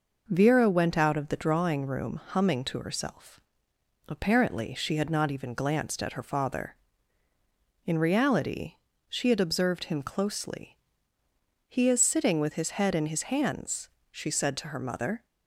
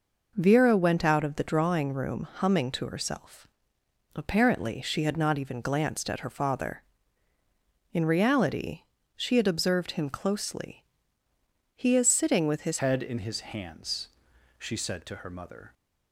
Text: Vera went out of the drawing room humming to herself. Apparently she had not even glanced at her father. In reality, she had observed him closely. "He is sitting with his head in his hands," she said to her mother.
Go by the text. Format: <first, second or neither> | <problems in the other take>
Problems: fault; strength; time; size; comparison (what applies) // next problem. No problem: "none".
first | changes voice at "head"; from 12.7 s on; 3.0 s long